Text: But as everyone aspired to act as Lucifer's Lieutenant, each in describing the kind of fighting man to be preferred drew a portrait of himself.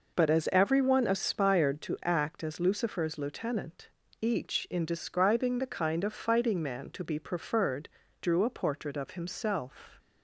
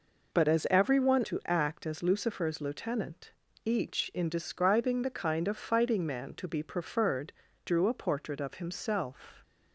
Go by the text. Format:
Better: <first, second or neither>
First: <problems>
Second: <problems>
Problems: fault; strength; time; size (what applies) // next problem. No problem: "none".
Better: first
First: pauses between "preferred" and "drew"; slight; at 7.8 s; 0.32 s long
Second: skips "aspired"; at 1.2 s // pauses between "preferred" and "drew"; slight; at 7.3 s; 0.32 s long